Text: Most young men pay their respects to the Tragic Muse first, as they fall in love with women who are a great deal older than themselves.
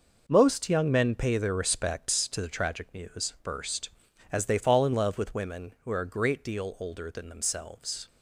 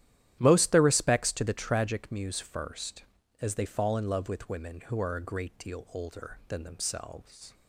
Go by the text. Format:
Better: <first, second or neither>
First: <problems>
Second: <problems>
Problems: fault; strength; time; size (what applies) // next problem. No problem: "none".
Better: first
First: none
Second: starts louder than the rest; strong; until 1.4 s; 12 dB // skips "young men pay"; at 0.7 s